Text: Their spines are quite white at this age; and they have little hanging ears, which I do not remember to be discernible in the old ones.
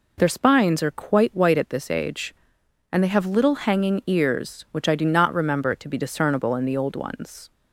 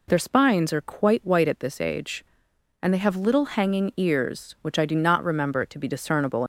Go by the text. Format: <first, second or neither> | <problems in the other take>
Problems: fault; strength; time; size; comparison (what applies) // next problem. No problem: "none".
first | stops before "in the old ones"; at 6.4 s